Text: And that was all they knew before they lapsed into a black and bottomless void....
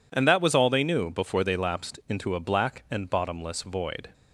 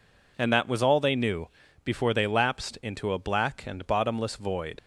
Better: first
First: none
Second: pauses between "knew" and "before"; slight; at 1.4 s; 0.36 s long // leaves "void" unfinished; at 4.7 s; 55 ms

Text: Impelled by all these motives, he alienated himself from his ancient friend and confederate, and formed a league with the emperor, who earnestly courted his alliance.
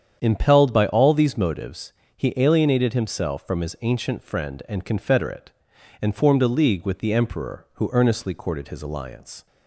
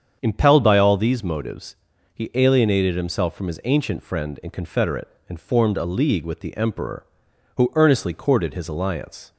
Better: neither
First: starts louder than the rest; strong; until 1.2 s; 8.5 dB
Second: starts louder than the rest; strong; until 1.2 s; 7.5 dB

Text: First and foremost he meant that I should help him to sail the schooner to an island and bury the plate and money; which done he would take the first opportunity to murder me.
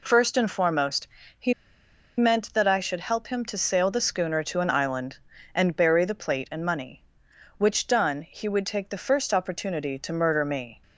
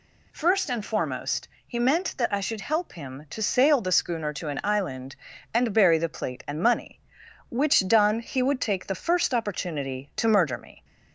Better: second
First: pauses between "foremost" and "he"; slight; at 1.0 s; 0.32 s long // pauses between "he" and "meant"; noticeable; at 1.5 s; 0.64 s long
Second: pauses between "foremost" and "he"; slight; at 1.4 s; 0.18 s long

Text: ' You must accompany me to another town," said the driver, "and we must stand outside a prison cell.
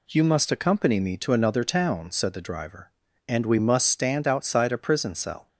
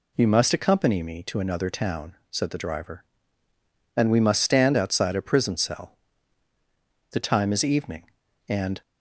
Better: first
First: none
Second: goes on to say "The time is evening and"; strong; from 7.1 s on; 1.7 s long

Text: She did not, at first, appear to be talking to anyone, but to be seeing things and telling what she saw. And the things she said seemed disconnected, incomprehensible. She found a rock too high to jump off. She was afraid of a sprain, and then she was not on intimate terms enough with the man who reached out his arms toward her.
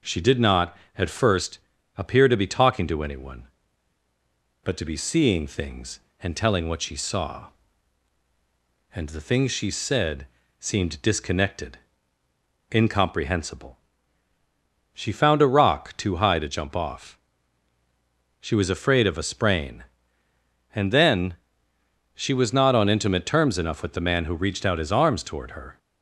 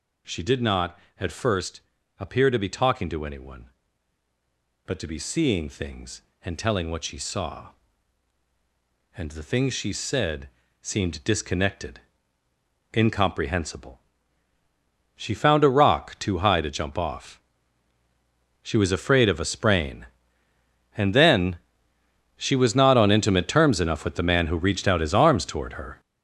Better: first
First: pauses between "said" and "seemed"; slight; at 10.2 s; 0.34 s long // pauses between "then" and "she"; noticeable; at 21.3 s; 0.78 s long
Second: gets louder; strong; throughout; 9 dB // pauses between "said" and "seemed"; slight; at 10.4 s; 0.34 s long // pauses between "then" and "she"; noticeable; at 21.5 s; 0.78 s long

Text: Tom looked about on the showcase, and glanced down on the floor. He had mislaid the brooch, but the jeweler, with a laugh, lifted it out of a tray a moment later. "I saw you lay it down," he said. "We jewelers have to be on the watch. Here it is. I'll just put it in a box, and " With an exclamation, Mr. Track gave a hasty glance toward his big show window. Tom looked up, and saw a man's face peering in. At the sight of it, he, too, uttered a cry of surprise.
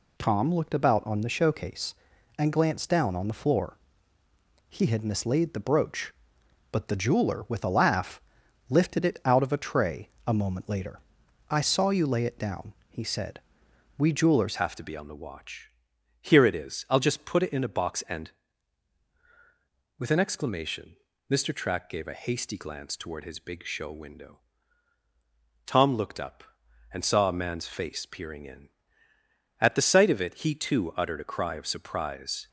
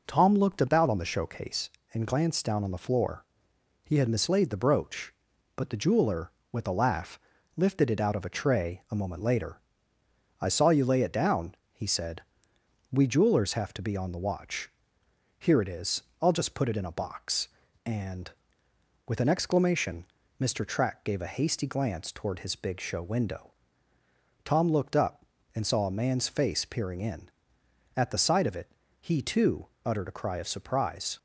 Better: second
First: pauses between "tray" and "a"; slight; at 10.0 s; 0.18 s long // changes voice at "have"; from 14.5 s on; 17.9 s long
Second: none

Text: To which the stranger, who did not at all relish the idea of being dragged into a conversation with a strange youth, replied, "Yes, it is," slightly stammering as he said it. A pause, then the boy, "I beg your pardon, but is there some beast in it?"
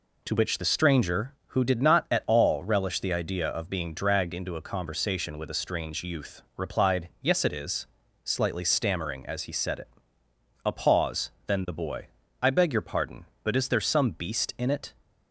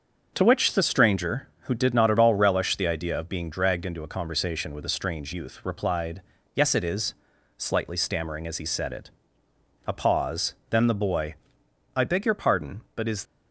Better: first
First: none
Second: starts louder than the rest; until 1.3 s; 7 dB // stops before "there some beast in it"; at 13.2 s

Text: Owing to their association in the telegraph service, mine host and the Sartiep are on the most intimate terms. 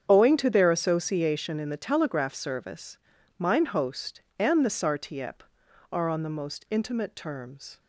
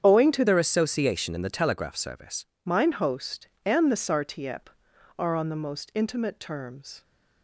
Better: first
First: starts louder than the rest; strong; until 1.0 s; 8 dB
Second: starts louder than the rest; strong; until 1.0 s; 8 dB // changes voice from "their" to "service"; from 0.4 to 2.4 s; 2.0 s long

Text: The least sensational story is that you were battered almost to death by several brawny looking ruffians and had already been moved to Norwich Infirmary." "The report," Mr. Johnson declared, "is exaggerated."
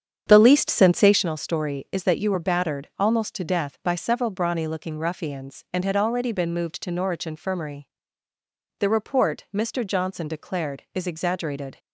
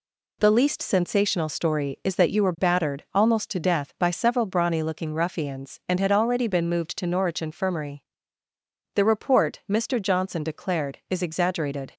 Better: second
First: starts louder than the rest; strong; until 1.3 s; 8 dB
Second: none

